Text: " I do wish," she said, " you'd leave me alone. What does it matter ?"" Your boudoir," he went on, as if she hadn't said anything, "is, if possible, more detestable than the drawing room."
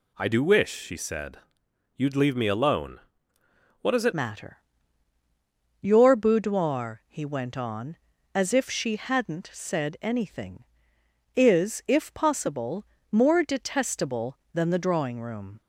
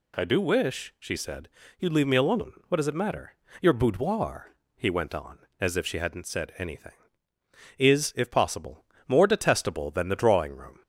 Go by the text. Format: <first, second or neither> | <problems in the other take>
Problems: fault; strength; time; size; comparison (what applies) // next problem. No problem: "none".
second | changes voice at "matter"; from 4.1 s on; 11.5 s long